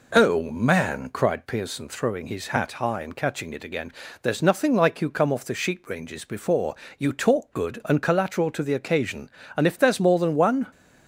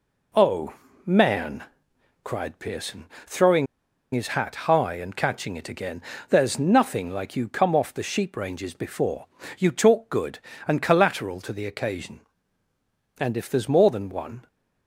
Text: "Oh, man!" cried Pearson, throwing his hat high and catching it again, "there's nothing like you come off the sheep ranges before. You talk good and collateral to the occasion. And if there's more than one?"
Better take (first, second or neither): first